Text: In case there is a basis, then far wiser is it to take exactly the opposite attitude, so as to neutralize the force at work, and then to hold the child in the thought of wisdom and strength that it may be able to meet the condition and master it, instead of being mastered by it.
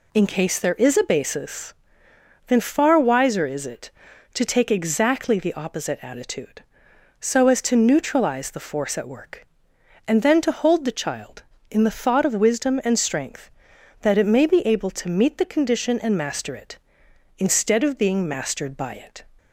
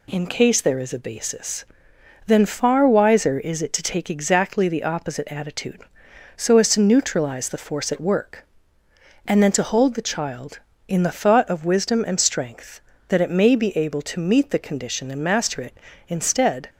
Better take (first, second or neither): first